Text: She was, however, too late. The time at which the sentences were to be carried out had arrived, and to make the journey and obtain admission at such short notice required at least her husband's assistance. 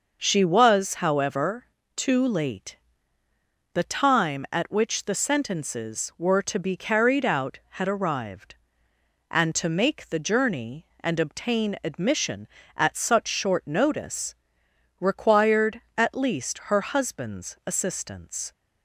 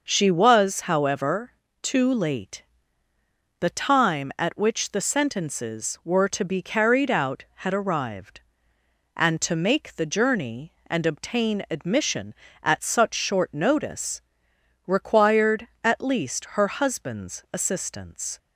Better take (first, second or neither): neither